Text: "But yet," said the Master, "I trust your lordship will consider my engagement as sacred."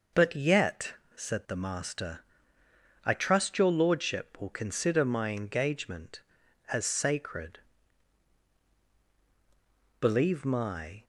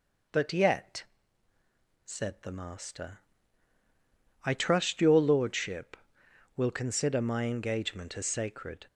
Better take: second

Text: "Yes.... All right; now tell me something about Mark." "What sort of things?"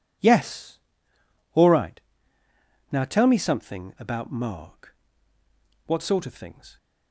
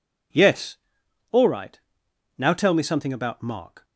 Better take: first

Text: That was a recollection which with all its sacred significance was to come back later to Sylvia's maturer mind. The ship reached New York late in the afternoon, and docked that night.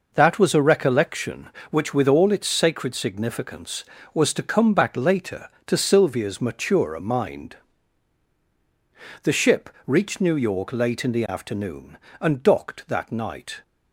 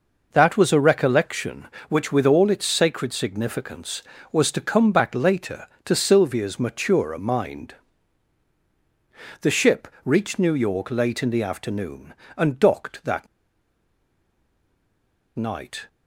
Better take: first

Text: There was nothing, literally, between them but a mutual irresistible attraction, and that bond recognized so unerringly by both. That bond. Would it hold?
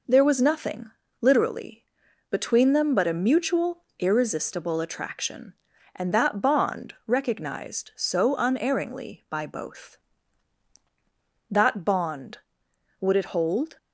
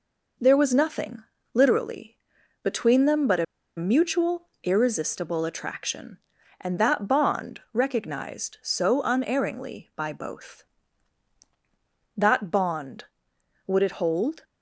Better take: first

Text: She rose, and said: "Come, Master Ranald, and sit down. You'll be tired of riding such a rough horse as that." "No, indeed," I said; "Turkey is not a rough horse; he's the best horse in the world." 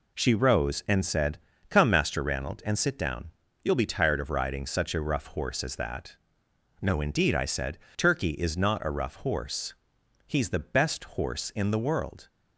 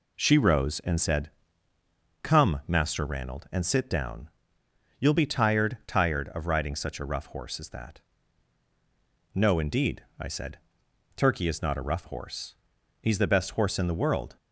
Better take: first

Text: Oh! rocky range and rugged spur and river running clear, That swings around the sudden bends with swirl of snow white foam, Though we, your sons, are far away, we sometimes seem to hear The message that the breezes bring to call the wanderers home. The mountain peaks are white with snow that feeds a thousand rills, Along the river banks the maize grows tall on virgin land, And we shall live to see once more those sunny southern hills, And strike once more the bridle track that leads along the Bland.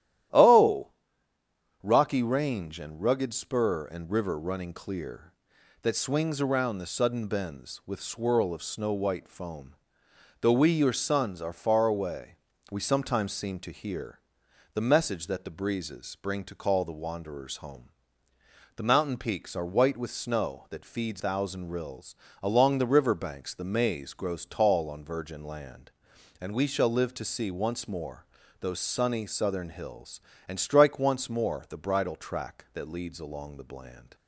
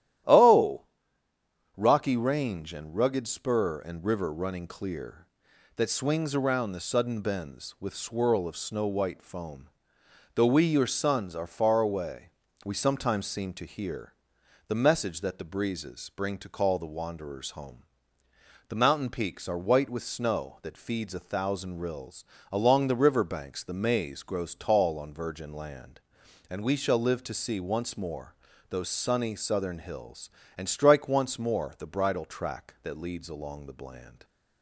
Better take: second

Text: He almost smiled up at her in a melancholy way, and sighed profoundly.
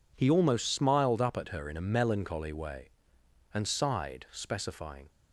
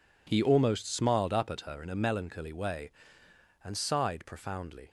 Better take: second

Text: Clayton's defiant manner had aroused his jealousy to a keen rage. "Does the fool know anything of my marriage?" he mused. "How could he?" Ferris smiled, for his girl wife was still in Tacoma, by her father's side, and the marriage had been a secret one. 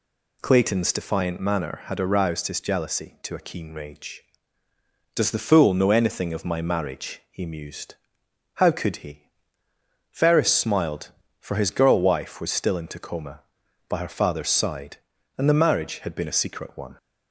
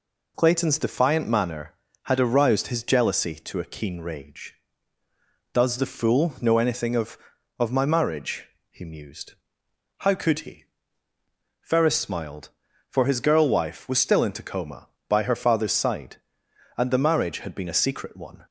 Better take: first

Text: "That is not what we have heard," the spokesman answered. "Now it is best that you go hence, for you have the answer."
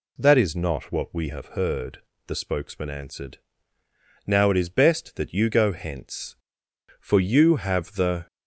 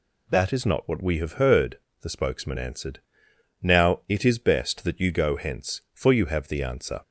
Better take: second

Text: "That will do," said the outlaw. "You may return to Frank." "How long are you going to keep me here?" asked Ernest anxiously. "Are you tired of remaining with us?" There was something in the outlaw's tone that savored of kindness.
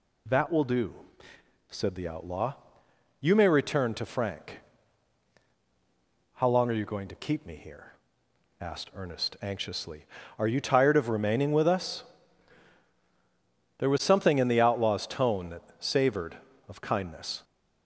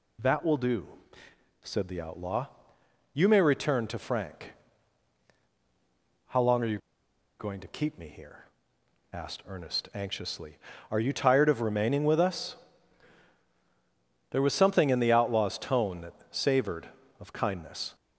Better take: first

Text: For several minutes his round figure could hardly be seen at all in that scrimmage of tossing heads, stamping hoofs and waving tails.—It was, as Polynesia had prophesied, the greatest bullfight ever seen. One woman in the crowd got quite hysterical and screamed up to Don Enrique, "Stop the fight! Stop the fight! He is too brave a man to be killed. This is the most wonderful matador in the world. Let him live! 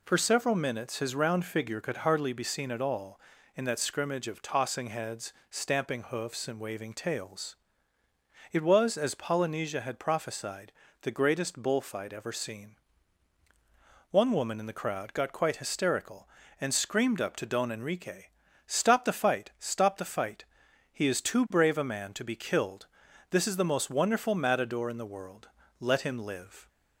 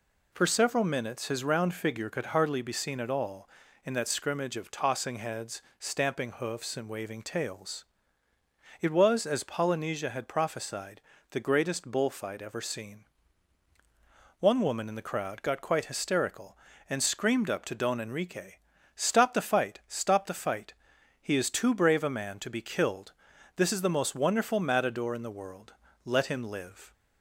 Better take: neither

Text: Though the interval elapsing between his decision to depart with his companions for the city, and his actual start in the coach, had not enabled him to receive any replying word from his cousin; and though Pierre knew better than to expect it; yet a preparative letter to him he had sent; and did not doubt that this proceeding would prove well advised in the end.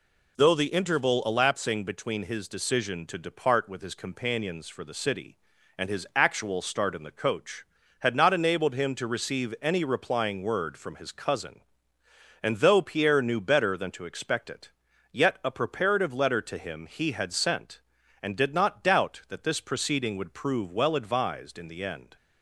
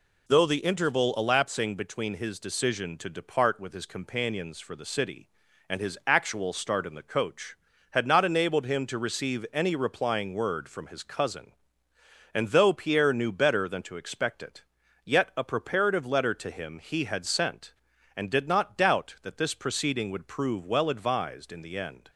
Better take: neither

